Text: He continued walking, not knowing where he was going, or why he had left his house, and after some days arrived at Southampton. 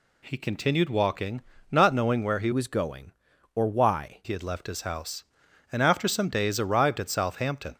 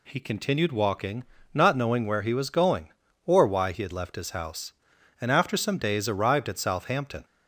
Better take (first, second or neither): second